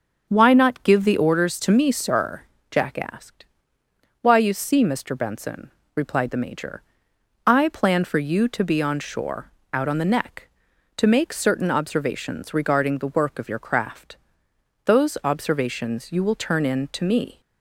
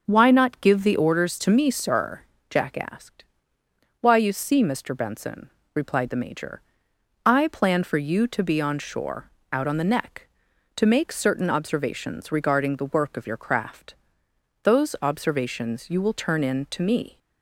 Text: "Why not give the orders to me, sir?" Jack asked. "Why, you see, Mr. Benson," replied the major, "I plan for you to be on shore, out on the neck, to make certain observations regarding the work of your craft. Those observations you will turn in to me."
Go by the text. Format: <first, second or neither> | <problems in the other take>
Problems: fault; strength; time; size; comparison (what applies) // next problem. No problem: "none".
neither | starts louder than the rest; the same in both